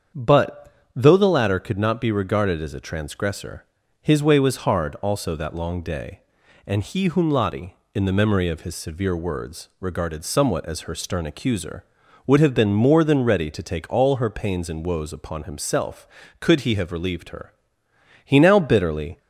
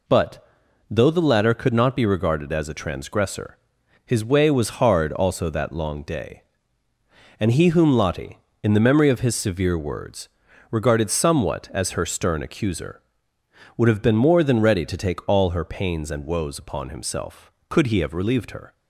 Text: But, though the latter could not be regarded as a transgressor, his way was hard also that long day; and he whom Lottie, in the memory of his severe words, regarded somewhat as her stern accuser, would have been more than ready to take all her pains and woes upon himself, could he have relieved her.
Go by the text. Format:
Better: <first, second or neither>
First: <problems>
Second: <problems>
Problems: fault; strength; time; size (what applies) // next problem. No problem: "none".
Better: second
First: starts louder than the rest; strong; until 1.3 s; 7 dB // goes on to say "He now bitterly"; noticeable; from 18.2 s on; 0.94 s long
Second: none